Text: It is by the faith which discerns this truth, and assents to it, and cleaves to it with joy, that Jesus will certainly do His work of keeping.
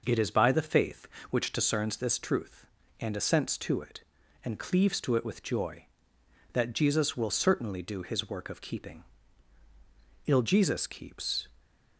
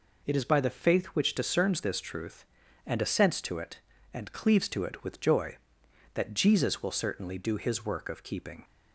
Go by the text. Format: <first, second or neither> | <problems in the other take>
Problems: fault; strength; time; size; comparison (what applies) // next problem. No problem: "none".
second | goes on to say "Ill Jesus keeps"; noticeable; from 10.2 s on; 1.2 s long